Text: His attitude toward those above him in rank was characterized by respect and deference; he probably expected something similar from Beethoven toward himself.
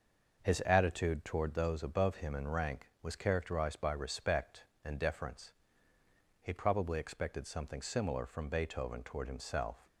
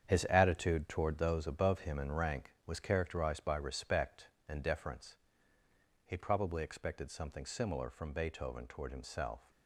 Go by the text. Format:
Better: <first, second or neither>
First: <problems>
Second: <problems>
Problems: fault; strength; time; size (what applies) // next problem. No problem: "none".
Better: first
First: none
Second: gets quieter; strong; throughout; 9 dB